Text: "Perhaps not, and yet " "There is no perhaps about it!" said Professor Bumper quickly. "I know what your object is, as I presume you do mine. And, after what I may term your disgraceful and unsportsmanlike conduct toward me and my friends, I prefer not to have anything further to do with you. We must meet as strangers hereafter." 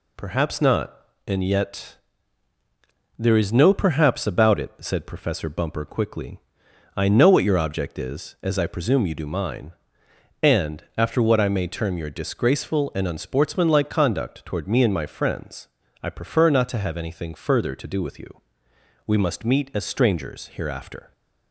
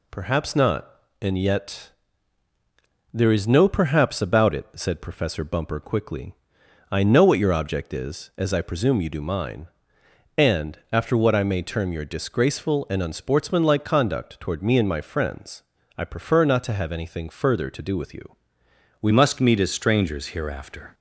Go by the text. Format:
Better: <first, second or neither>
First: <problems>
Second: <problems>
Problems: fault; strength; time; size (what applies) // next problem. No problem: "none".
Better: first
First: none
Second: changes voice at "must"; from 19.1 s on; 1.8 s long